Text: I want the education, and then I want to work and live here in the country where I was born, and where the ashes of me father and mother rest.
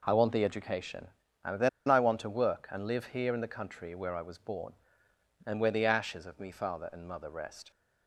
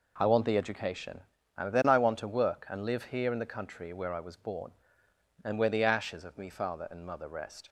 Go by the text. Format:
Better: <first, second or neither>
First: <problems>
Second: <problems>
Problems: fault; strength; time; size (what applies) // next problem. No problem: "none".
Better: second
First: pauses between "then" and "I"; slight; at 1.6 s; 0.19 s long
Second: none